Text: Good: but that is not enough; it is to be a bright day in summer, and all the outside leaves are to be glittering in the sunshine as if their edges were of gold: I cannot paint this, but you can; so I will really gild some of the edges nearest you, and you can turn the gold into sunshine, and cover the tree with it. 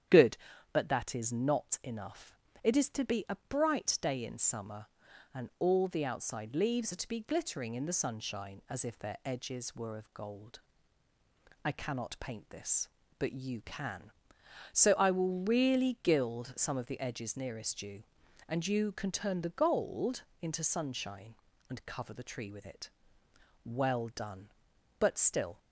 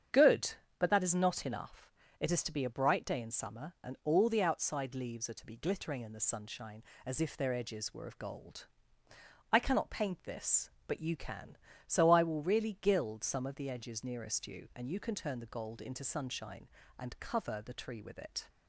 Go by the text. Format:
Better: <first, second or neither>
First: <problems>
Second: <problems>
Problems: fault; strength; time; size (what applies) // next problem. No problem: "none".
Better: second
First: starts louder than the rest; strong; until 1.4 s; 9.5 dB // pauses between "gold" and "into"; slight; at 20.2 s; 0.18 s long // goes on to say "Well done but still"; strong; from 23.7 s on; 1.8 s long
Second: starts louder than the rest; strong; until 1.3 s; 8 dB